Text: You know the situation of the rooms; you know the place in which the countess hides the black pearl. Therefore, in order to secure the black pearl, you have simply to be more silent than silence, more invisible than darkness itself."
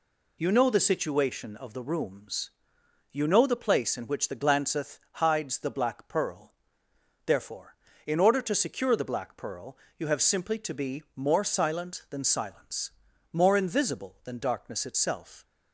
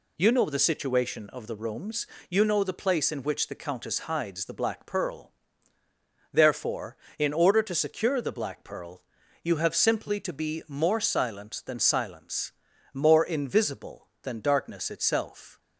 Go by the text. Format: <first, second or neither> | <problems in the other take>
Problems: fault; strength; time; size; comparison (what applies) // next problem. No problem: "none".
second | says "glanceth" for "countess"; at 4.3 s